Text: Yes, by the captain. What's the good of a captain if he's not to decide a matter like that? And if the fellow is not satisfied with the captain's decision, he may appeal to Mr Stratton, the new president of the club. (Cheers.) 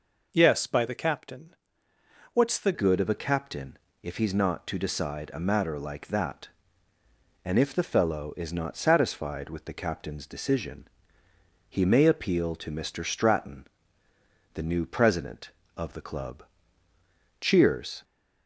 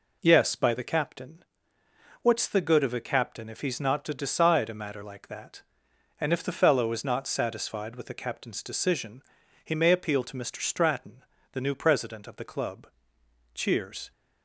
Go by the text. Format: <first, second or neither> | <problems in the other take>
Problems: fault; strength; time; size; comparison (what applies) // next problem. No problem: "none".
second | changes voice at "good"; from 2.7 s on; 15.3 s long // pauses between "captain" and "if"; slight; at 3.7 s; 0.26 s long